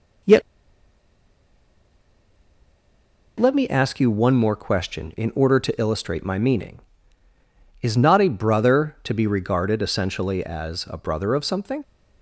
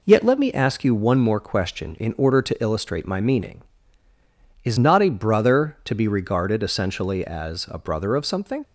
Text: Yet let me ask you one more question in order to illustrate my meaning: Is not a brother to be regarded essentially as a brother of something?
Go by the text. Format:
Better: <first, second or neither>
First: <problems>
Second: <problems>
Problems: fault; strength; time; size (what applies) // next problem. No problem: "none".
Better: second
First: pauses between "Yet" and "let"; strong; at 0.4 s; 2.9 s long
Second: none